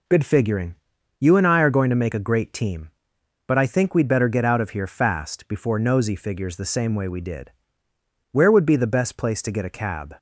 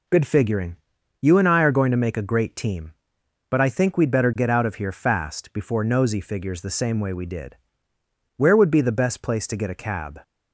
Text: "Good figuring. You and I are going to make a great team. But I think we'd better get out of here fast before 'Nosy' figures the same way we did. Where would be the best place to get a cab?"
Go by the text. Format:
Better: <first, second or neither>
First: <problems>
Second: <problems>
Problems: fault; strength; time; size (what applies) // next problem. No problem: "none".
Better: neither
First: none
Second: none